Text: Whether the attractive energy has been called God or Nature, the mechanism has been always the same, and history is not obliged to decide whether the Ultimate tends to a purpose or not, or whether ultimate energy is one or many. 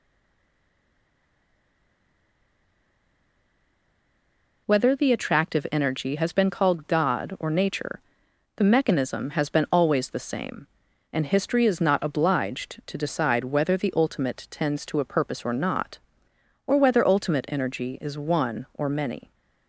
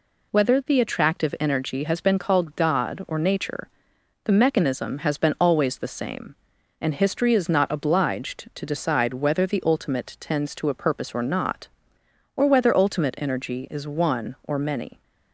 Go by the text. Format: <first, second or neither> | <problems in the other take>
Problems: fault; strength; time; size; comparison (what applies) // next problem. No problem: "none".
second | stays silent before the first word; strong; until 4.6 s; 4.6 s long